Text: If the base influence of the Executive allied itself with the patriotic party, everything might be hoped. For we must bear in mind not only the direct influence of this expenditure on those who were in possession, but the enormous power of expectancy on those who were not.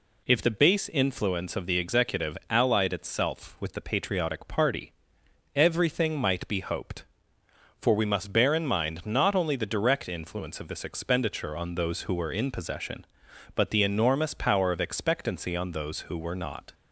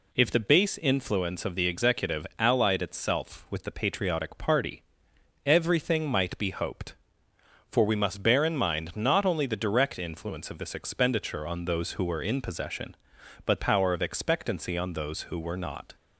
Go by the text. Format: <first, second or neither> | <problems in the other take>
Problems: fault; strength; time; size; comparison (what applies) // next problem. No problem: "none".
first | skips "the enormous"; at 13.6 s